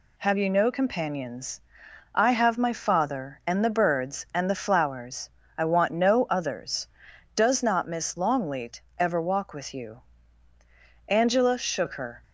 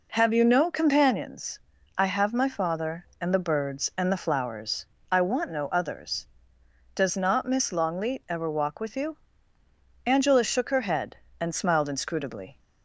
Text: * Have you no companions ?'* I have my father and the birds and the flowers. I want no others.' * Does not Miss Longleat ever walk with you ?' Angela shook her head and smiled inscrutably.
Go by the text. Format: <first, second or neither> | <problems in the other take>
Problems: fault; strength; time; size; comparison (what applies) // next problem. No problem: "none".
second | pauses between "Longleat" and "ever"; slight; at 8.8 s; 0.18 s long // stops before "head and smiled inscrutably"; at 12.2 s